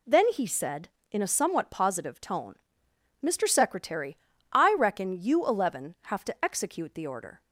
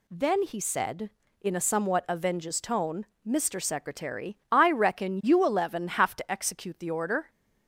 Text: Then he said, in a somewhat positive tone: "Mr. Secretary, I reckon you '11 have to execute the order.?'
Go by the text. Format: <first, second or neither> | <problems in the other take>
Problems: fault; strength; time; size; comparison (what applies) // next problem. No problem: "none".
first | says "avenges" for "positive"; at 2.0 s